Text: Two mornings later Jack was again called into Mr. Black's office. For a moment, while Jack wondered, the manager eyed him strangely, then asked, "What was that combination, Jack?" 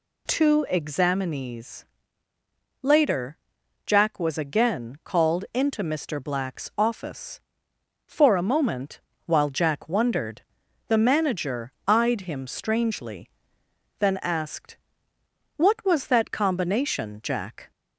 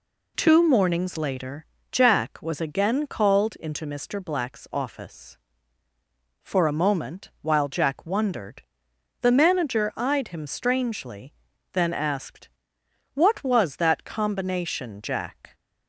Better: second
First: says "examinees" for "mornings"; at 0.7 s // pauses between "later" and "Jack"; noticeable; at 3.3 s; 0.48 s long // pauses between "manager" and "eyed"; slight; at 11.7 s; 0.16 s long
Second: pauses between "later" and "Jack"; slight; at 1.6 s; 0.28 s long

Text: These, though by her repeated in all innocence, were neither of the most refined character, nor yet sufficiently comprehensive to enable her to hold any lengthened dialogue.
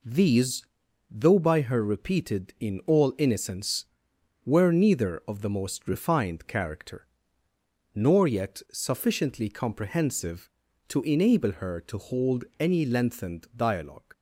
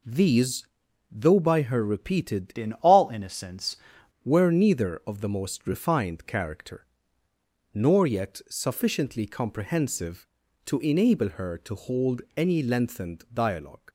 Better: first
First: pauses between "hold" and "any"; slight; at 12.4 s; 0.16 s long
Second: changes voice from "in" to "innocence"; from 2.5 to 3.7 s; 1.2 s long // pauses between "hold" and "any"; slight; at 12.2 s; 0.16 s long

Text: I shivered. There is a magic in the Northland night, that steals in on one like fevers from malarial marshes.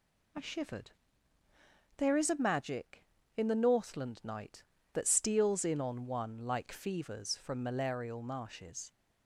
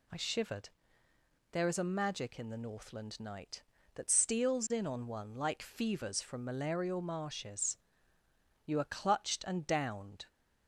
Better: first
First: none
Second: goes on to say "You are clutched and downed"; from 8.6 s on; 1.6 s long

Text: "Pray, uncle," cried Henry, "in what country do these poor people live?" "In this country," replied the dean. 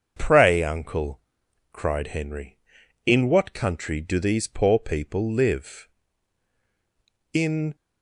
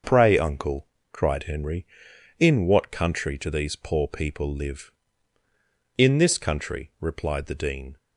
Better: second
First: starts louder than the rest; until 1.1 s; 7 dB // stops before "this country replied the dean"; at 7.7 s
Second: starts louder than the rest; until 1.3 s; 6 dB

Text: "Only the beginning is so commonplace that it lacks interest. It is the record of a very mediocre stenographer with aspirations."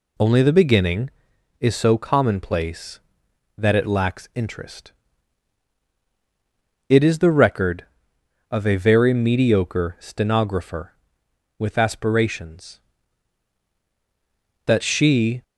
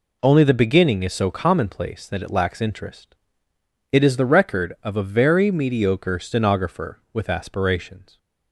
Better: second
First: goes on to say "That she"; noticeable; from 14.6 s on; 0.78 s long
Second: none

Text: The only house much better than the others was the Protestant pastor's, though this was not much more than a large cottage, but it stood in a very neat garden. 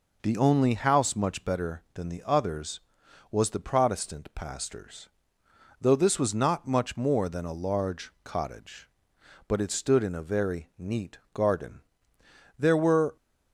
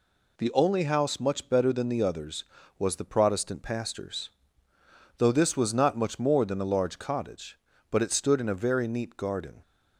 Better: second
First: goes on to say "There were"; from 12.5 s on; 0.58 s long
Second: none

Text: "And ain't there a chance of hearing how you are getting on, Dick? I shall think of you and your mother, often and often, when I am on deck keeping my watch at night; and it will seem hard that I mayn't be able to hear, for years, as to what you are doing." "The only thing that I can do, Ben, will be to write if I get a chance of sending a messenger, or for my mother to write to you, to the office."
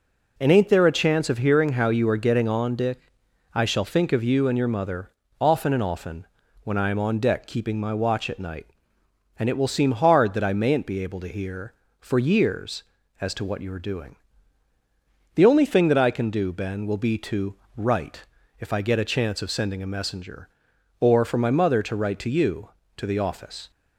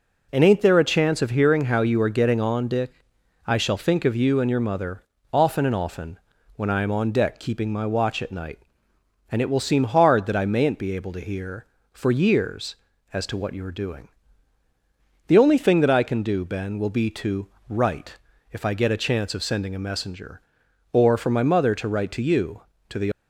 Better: first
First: pauses between "to" and "write"; slight; at 17.5 s; 0.20 s long // pauses between "write" and "if"; slight; at 18.2 s; 0.36 s long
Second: pauses between "to" and "write"; slight; at 17.4 s; 0.20 s long // pauses between "write" and "if"; slight; at 18.1 s; 0.36 s long // stops before "office"; at 23.1 s

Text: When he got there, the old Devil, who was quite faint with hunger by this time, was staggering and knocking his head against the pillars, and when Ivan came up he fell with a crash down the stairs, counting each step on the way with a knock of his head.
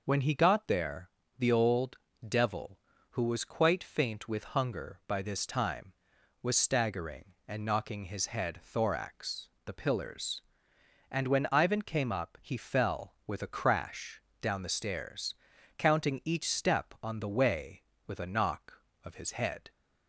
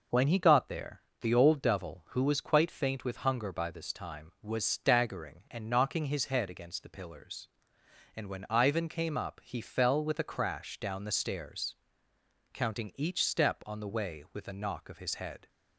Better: second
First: pauses between "old" and "Devil"; slight; at 1.9 s; 0.30 s long // says "thorax" for "against"; at 8.6 s // pauses between "crash" and "down"; slight; at 14.1 s; 0.22 s long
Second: none

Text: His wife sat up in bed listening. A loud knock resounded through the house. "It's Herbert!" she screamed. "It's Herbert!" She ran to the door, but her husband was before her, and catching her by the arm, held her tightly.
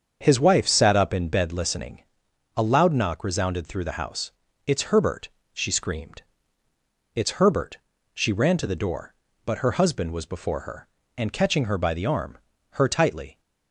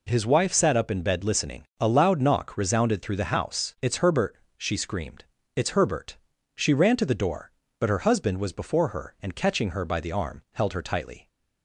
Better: second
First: starts louder than the rest; strong; until 1.2 s; 7 dB // skips "held"; at 12.5 s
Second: none

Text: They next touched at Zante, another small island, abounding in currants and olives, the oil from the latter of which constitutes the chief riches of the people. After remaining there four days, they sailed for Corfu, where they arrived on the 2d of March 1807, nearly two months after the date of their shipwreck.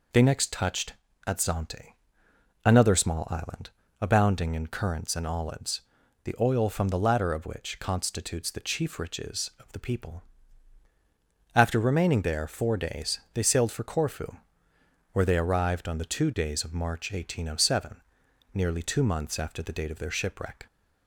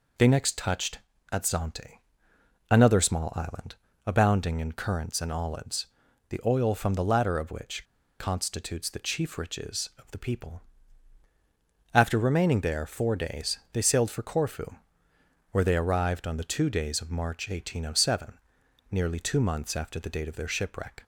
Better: first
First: none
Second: pauses between "which" and "constitutes"; slight; at 7.8 s; 0.35 s long

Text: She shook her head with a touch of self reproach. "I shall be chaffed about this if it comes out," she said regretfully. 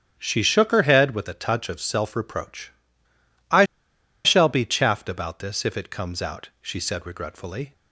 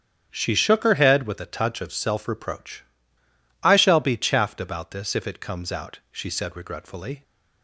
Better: second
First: starts louder than the rest; strong; until 1.1 s; 9 dB // pauses between "I" and "shall"; noticeable; at 3.6 s; 0.60 s long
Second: starts louder than the rest; strong; until 1.3 s; 9 dB

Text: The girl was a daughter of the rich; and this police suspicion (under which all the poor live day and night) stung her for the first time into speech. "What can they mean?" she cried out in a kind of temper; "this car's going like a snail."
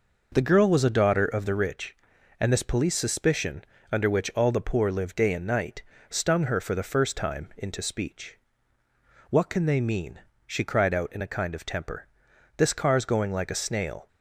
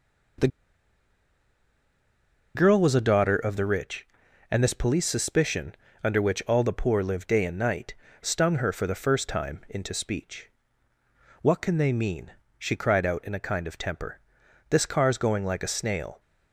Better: first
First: none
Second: pauses between "The" and "girl"; strong; at 0.4 s; 2.0 s long

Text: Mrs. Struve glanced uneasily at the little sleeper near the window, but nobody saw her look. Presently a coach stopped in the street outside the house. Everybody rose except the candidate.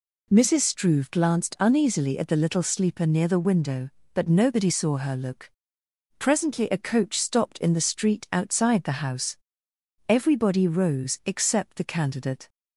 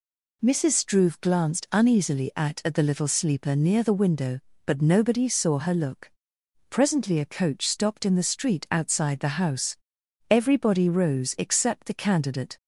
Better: first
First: none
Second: says "at" twice; at 2.6 s

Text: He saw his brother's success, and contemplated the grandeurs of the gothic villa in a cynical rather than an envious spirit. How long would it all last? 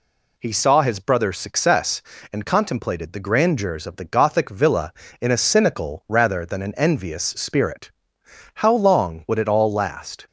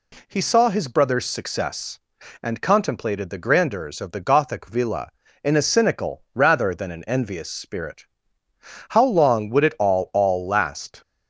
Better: first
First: none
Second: says "all" twice; at 10.1 s

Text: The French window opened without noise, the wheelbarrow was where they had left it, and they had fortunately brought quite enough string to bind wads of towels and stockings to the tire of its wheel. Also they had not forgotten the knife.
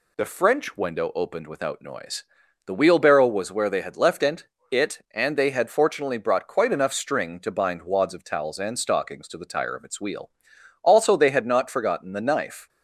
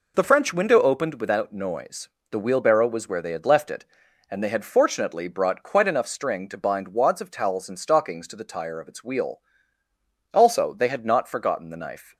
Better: second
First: says "it" twice; at 4.7 s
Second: none

